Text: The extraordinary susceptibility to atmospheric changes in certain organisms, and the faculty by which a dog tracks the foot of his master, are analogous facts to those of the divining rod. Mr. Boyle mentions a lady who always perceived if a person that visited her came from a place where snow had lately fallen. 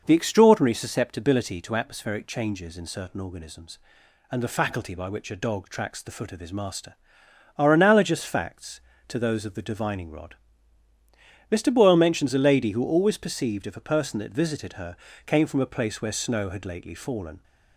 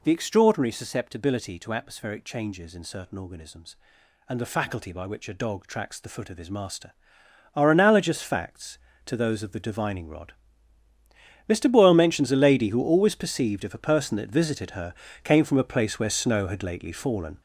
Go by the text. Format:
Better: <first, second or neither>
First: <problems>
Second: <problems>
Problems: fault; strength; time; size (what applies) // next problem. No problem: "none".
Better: first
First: pauses between "her" and "came"; slight; at 14.9 s; 0.28 s long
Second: gets louder; strong; throughout; 7.5 dB // pauses between "her" and "came"; slight; at 14.9 s; 0.28 s long